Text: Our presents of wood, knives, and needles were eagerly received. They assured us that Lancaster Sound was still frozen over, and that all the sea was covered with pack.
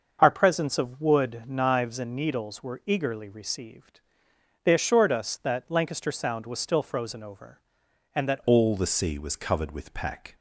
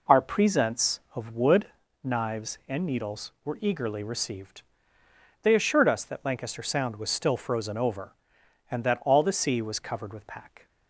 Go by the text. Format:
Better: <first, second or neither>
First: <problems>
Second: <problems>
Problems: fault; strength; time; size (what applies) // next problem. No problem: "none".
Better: second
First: starts louder than the rest; until 1.2 s; 6.5 dB // changes voice at "all"; from 8.4 s on; 1.9 s long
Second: none